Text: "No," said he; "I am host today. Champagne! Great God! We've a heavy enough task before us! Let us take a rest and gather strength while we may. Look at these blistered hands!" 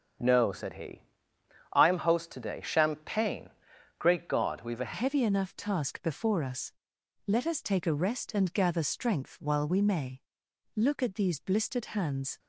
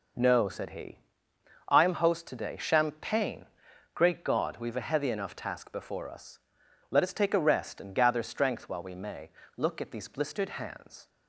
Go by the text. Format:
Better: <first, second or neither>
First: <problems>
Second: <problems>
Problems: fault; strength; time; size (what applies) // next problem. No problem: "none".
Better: second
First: starts louder than the rest; strong; until 1.8 s; 7 dB // changes voice at "heavy"; from 4.9 s on; 7.4 s long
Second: none